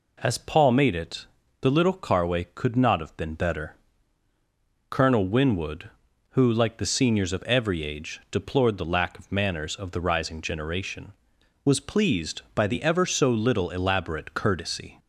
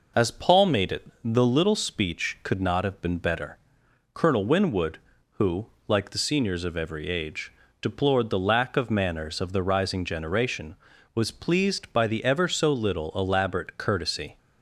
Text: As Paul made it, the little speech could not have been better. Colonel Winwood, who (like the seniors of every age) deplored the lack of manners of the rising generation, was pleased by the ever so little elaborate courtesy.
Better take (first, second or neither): second